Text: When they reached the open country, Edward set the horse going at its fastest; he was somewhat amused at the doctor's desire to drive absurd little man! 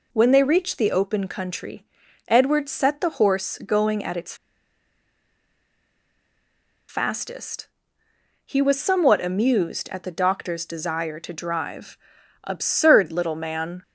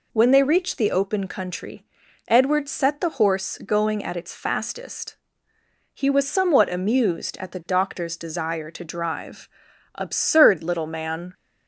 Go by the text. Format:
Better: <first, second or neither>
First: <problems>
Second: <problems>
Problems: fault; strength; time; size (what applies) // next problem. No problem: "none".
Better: second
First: pauses between "its" and "fastest"; strong; at 4.3 s; 2.5 s long // pauses between "drive" and "absurd"; noticeable; at 11.9 s; 0.46 s long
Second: pauses between "drive" and "absurd"; noticeable; at 9.4 s; 0.46 s long